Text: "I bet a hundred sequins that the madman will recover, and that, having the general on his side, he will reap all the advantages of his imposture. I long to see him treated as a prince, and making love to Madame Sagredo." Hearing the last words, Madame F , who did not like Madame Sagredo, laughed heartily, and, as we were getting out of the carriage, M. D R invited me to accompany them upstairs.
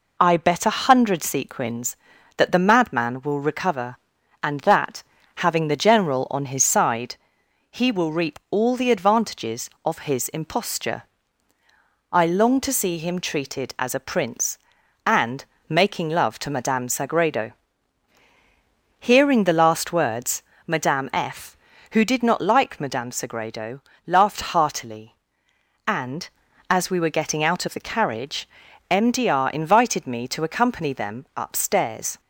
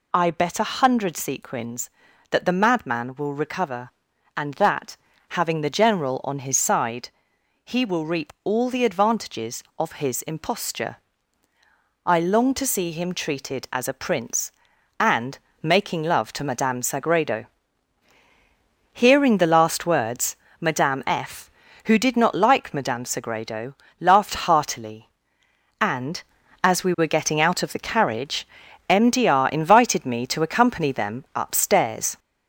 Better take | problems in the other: first | gets louder; throughout; 3.5 dB // pauses between "and" and "making"; slight; at 15.3 s; 0.24 s long; slight in the first

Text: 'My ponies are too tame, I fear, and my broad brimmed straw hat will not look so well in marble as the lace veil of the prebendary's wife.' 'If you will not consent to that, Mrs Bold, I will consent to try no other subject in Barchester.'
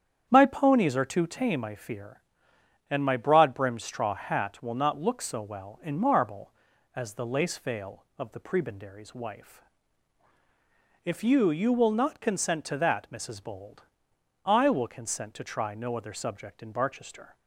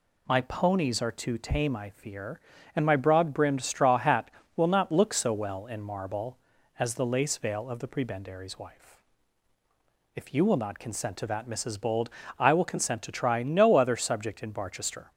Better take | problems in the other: second | starts louder than the rest; strong; until 1.3 s; 8.5 dB // says "you" twice; at 11.4 s

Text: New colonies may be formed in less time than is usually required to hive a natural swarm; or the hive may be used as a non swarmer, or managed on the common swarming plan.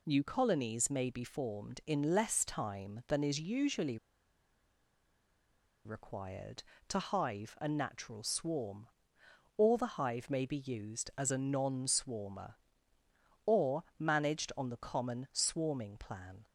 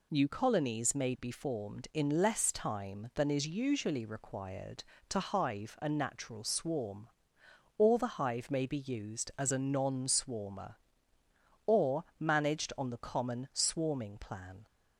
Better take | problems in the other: second | pauses between "usually" and "required"; strong; at 3.9 s; 1.8 s long // pauses between "or" and "managed"; slight; at 13.8 s; 0.16 s long; slight in the second

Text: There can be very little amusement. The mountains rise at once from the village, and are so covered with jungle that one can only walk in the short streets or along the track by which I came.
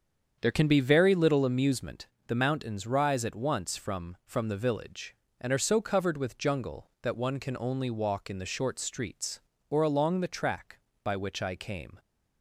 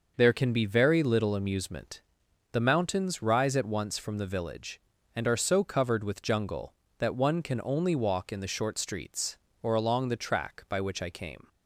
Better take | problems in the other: second | starts louder than the rest; strong; until 1.4 s; 7.5 dB // says "from" twice; at 4.2 s

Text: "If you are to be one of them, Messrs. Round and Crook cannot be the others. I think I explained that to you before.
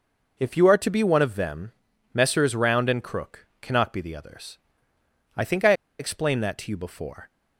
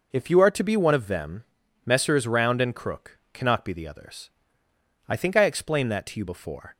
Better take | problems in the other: second | pauses between "Crook" and "cannot"; slight; at 3.4 s; 0.16 s long; slight in the second // pauses between "I" and "explained"; slight; at 5.7 s; 0.26 s long

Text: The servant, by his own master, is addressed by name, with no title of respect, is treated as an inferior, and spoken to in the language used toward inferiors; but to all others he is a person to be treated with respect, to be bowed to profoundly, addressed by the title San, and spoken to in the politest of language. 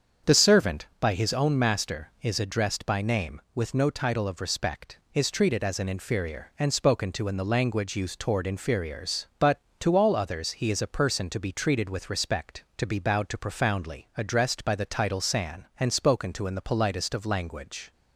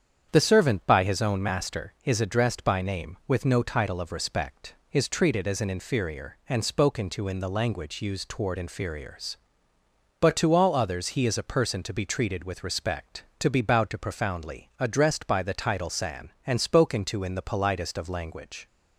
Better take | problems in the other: neither | starts louder than the rest; strong; the same in both

